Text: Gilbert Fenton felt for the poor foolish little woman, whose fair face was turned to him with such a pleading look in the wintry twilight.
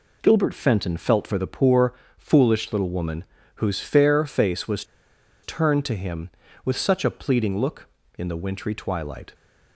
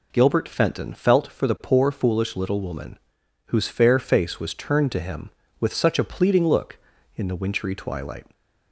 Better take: second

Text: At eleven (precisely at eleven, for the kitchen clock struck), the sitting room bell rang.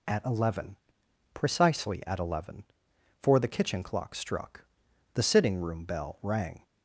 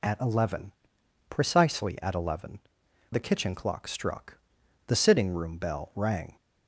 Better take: first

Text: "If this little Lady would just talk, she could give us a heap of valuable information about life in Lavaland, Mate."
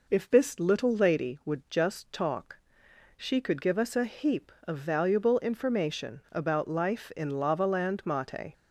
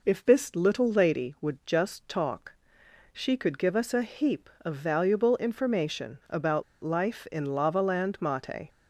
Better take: first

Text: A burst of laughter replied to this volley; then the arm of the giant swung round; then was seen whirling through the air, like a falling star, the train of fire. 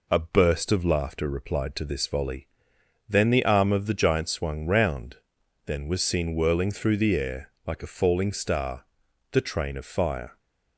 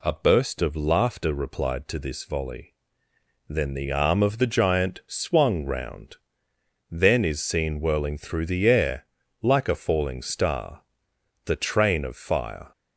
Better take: first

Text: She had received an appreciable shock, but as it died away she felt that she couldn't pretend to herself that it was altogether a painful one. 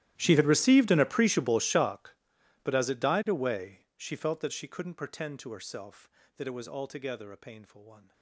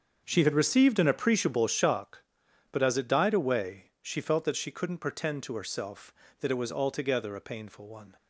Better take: second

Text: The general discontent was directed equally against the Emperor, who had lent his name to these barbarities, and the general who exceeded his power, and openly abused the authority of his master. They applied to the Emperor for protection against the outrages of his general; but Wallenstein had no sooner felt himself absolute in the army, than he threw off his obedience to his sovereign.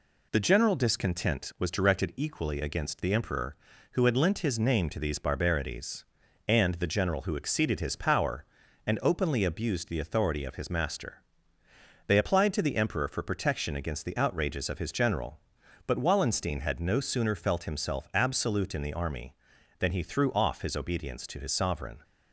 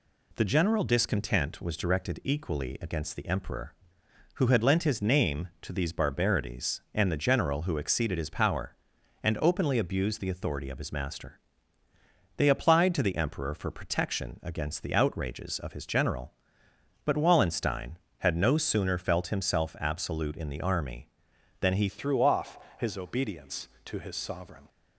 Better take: first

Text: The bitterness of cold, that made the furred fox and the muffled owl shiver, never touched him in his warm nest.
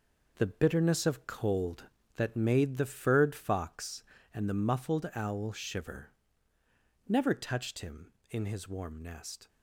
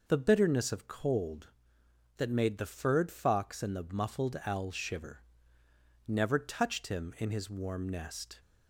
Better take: second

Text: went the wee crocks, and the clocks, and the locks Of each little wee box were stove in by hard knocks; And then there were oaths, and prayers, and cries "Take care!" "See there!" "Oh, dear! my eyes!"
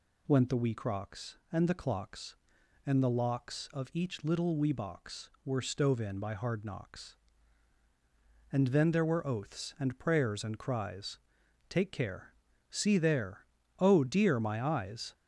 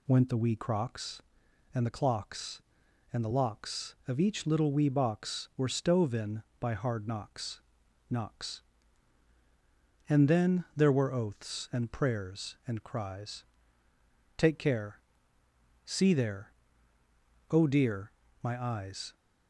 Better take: first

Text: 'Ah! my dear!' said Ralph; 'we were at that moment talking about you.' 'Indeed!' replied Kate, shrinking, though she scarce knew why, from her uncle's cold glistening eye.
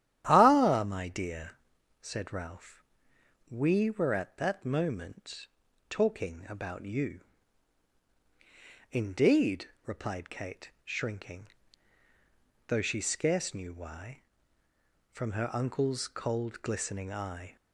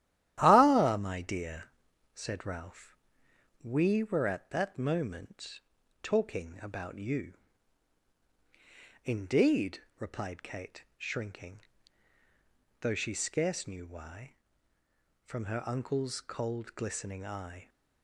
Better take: first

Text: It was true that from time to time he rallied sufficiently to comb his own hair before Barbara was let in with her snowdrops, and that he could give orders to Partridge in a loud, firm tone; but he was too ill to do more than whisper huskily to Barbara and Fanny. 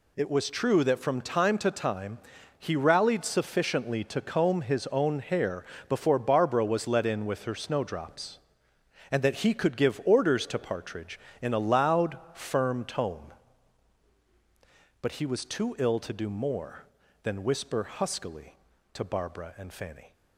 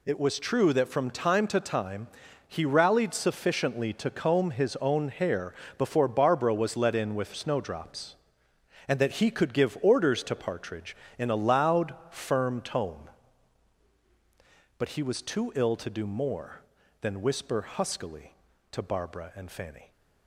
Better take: first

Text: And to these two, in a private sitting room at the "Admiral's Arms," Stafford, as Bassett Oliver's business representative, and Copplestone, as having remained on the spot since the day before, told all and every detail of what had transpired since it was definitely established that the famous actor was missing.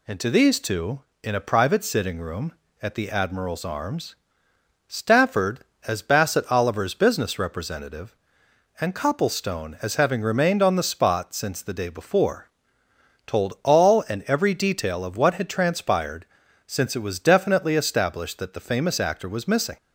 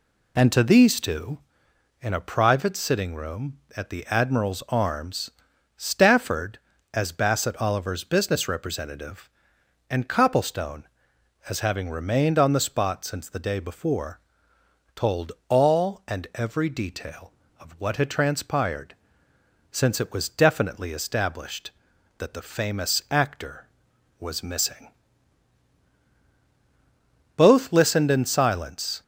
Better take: first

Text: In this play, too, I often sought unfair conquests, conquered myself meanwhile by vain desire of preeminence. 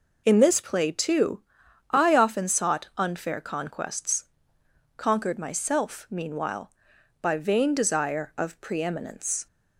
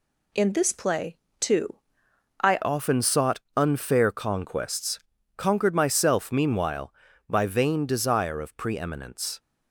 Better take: first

